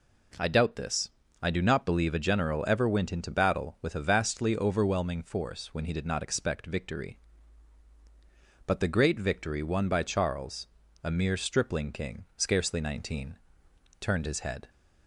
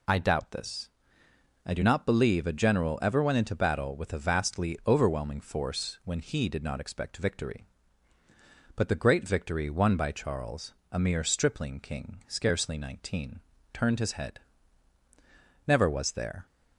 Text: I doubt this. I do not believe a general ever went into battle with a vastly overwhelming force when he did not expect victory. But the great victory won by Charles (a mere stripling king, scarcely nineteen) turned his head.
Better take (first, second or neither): first